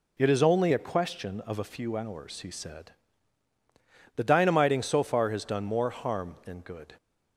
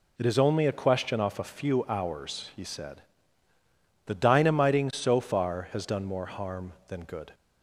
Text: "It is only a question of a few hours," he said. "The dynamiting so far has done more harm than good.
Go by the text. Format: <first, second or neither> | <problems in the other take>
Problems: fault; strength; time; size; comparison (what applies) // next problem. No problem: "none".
first | says "off" for "of"; at 1.1 s